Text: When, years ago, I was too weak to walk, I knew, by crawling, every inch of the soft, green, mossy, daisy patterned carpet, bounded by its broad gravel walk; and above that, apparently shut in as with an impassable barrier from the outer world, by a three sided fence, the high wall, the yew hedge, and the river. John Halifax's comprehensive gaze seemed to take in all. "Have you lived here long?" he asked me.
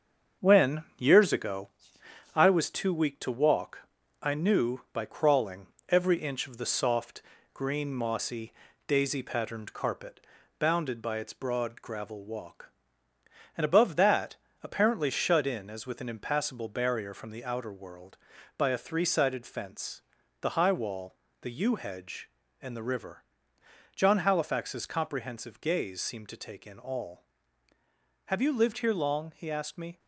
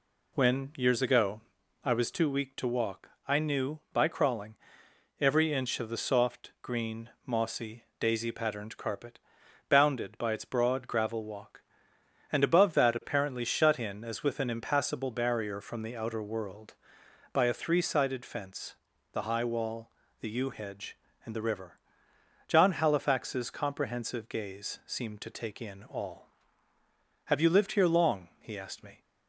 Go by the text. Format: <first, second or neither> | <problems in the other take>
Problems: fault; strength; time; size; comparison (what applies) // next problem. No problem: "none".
second | gets quieter; noticeable; throughout; 5.5 dB